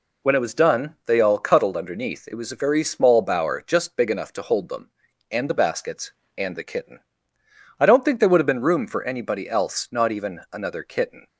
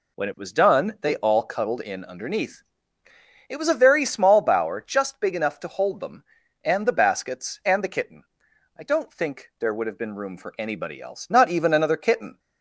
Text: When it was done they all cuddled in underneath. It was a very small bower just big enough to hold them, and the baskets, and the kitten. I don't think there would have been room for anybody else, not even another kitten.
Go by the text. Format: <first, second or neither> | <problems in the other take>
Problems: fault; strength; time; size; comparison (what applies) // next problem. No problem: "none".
second | skips "in"; at 1.7 s